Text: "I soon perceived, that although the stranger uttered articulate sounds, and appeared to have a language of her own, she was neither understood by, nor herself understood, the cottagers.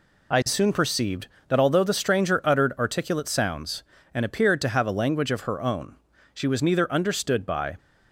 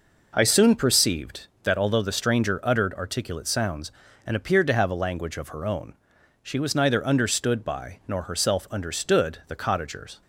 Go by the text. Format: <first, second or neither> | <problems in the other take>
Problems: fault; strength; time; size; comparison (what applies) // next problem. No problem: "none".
second | stops before "nor herself understood the cottagers"; at 7.7 s